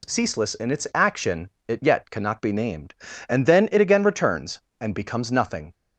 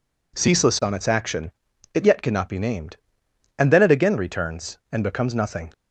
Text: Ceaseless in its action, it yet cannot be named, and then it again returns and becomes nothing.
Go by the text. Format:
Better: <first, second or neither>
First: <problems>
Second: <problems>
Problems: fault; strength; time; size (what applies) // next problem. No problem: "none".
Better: first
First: none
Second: says "on" for "in"; at 0.8 s